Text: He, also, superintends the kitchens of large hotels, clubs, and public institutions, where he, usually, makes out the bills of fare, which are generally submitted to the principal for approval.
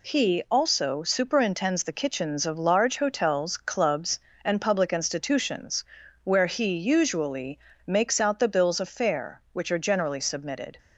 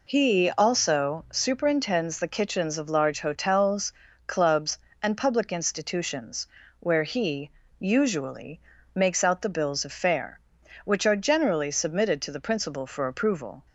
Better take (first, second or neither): second